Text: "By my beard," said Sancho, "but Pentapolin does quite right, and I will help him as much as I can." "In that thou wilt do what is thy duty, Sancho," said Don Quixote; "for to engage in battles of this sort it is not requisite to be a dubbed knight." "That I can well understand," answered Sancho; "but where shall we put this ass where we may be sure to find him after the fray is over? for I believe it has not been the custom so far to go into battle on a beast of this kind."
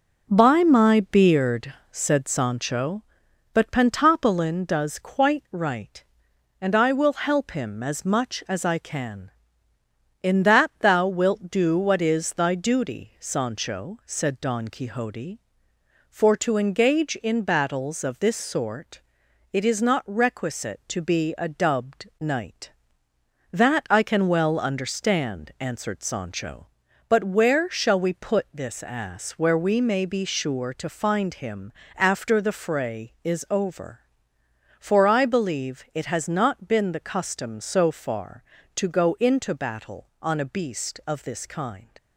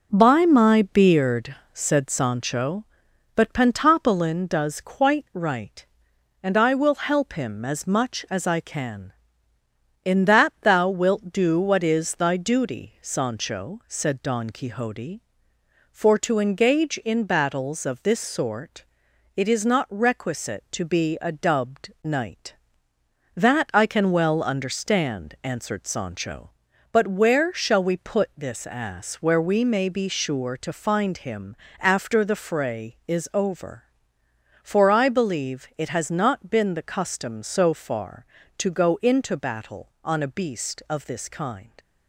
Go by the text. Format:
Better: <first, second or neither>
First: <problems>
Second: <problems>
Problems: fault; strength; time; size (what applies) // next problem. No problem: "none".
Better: neither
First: pauses between "sort" and "it"; noticeable; at 19.0 s; 0.52 s long // pauses between "him" and "after"; slight; at 31.7 s; 0.26 s long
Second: pauses between "sort" and "it"; noticeable; at 18.8 s; 0.52 s long // pauses between "him" and "after"; slight; at 31.5 s; 0.26 s long